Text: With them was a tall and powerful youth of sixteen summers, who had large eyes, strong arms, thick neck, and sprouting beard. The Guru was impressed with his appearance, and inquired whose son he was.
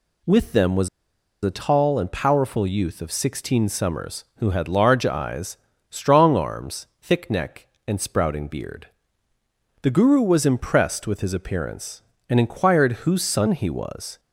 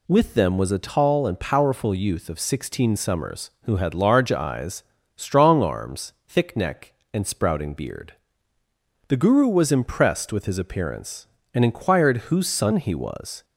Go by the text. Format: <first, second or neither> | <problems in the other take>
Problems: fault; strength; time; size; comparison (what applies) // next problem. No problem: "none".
second | pauses between "was" and "a"; noticeable; at 0.8 s; 0.54 s long